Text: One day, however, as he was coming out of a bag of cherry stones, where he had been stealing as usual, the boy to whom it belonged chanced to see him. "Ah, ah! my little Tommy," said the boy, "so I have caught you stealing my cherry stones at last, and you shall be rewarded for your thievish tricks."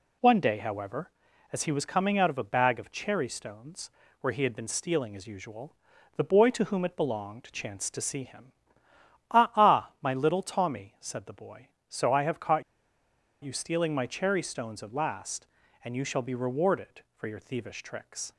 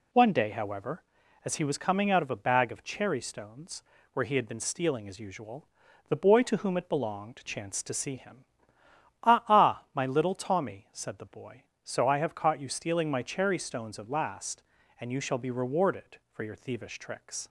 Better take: second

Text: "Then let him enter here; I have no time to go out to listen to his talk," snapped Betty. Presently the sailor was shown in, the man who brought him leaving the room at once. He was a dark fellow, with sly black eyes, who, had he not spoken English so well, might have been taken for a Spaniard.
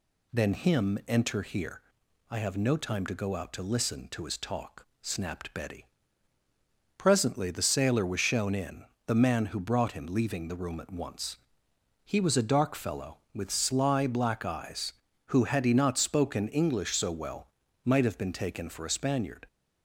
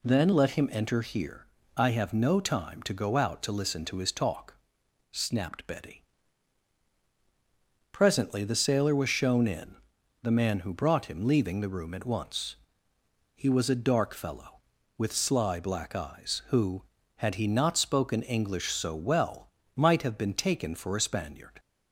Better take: second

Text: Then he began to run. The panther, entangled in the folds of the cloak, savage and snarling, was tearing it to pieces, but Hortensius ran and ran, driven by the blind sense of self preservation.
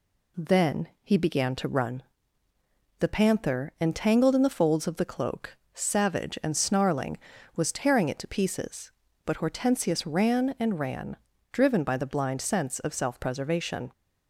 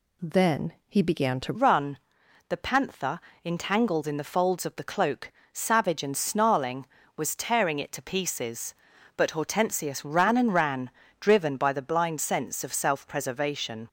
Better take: first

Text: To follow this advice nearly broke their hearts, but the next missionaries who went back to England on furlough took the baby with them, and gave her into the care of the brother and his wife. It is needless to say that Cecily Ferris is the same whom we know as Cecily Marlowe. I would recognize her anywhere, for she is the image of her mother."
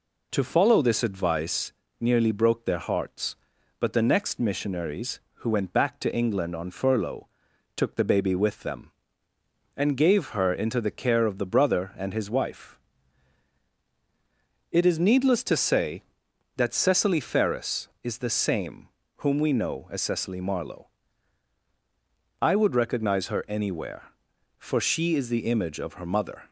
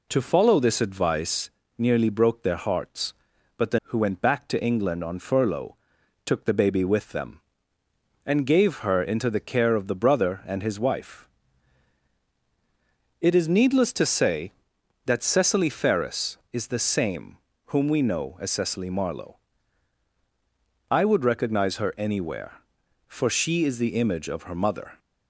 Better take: first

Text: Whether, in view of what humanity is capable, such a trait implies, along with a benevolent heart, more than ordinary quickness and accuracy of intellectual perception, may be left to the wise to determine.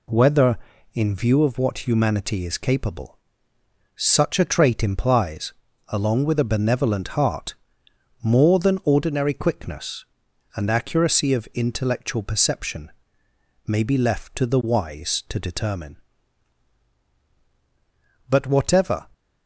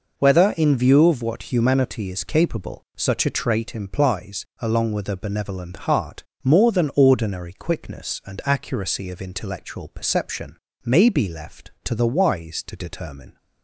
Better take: second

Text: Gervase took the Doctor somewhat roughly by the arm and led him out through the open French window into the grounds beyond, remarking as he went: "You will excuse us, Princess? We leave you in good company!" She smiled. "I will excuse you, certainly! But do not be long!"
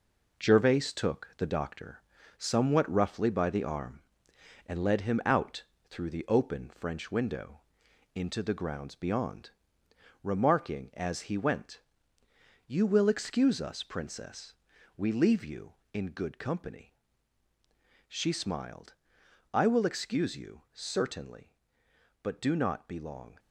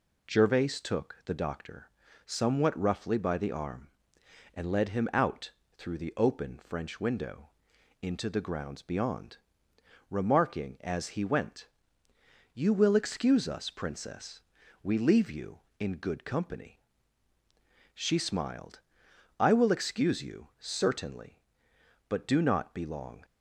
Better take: second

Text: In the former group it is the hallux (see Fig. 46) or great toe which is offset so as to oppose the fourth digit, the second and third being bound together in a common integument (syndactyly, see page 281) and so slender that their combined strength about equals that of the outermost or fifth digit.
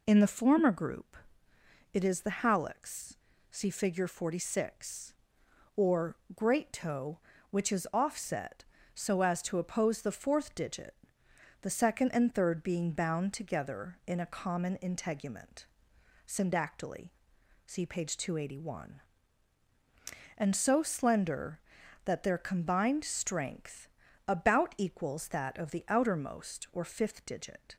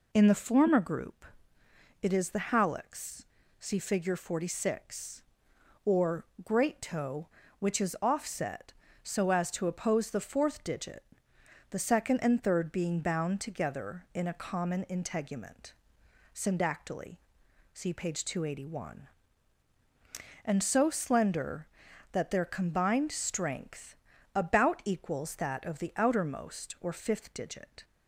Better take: neither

